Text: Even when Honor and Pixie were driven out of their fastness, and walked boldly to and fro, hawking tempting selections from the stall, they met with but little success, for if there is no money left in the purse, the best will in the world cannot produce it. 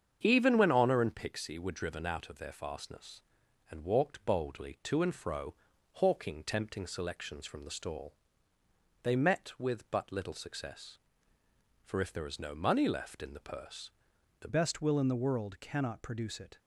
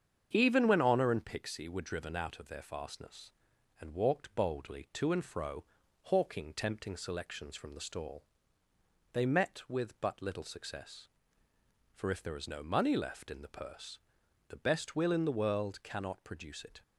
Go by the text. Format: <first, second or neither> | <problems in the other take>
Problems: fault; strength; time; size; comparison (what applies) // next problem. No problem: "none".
second | starts louder than the rest; strong; until 1.2 s; 7.5 dB; strong in the second // changes voice at "best"; from 14.4 s on; 2.1 s long